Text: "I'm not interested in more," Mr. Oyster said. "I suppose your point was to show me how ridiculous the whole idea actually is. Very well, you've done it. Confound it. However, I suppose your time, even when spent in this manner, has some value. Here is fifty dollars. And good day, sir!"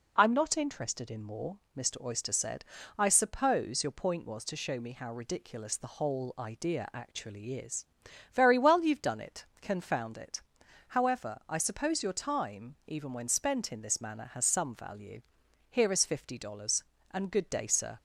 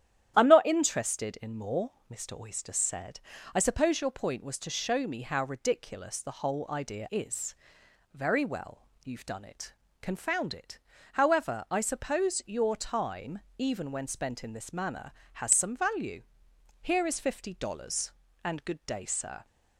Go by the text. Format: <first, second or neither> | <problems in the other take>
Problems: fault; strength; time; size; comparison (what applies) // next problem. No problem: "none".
first | starts louder than the rest; strong; until 1.3 s; 11 dB // skips "actually"; at 7.0 s